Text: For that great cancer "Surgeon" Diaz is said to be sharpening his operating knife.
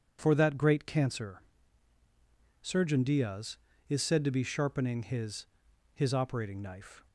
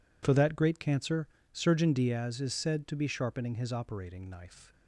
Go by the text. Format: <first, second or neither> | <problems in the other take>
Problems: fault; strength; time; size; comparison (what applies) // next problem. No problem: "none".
second | pauses between "cancer" and "Surgeon"; at 1.3 s; 1.2 s long; slight in the second // says "his" twice; at 5.9 s